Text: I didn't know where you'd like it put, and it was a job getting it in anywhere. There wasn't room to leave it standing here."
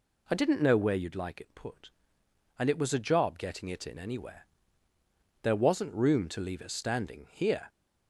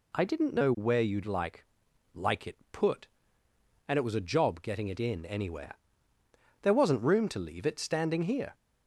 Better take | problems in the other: first | says "like" twice; at 2.1 s

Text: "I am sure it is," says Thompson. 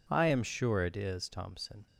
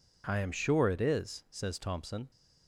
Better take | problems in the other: second | skips "says"; at 1.2 s

